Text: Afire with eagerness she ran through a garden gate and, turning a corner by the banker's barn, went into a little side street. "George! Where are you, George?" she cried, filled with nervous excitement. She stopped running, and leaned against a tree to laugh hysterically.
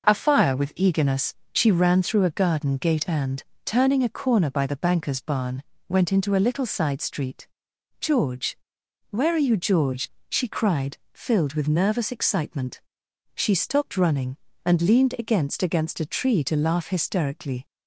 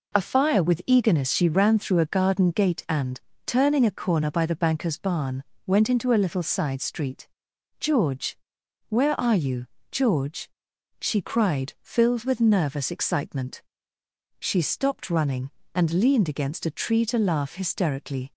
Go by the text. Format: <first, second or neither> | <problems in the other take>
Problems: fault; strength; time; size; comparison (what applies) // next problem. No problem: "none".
second | pauses between "eagerness" and "she"; slight; at 1.3 s; 0.20 s long // says "against" twice; at 15.6 s